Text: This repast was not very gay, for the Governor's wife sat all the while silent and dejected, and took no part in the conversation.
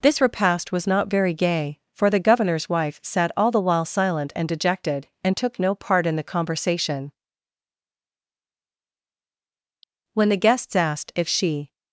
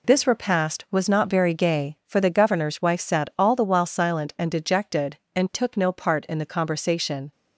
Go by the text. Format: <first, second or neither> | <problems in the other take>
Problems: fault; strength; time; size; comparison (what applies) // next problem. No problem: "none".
second | goes on to say "When the guests asked if she"; from 10.1 s on; 1.6 s long